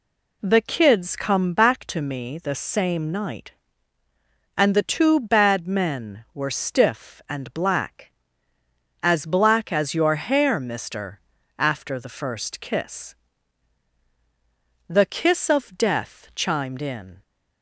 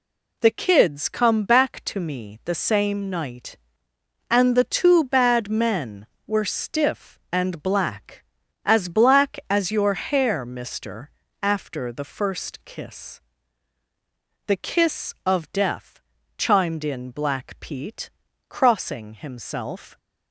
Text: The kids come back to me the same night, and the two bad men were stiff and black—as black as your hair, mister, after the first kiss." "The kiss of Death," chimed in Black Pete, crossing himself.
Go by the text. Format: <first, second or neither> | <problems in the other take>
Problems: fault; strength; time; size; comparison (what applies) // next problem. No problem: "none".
second | stops before "Black Pete crossing himself"; at 17.2 s